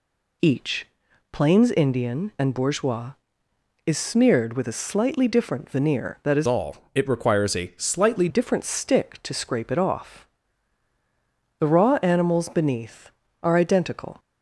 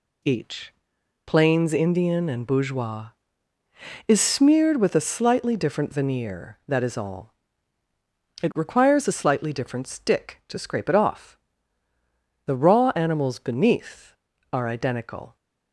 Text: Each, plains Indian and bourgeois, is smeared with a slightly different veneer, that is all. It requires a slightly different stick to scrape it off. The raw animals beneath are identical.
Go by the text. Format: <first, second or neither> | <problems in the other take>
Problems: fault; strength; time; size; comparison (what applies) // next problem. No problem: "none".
second | changes voice from "all" to "slightly"; from 6.4 to 8.2 s; 1.8 s long